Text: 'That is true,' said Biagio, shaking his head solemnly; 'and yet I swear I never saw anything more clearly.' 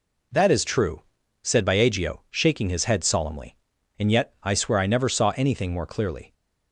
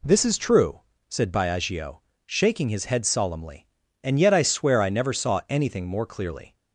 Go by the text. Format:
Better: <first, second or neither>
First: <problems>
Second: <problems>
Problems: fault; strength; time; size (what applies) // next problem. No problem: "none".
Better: first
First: none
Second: says "This" for "That"; at 0.0 s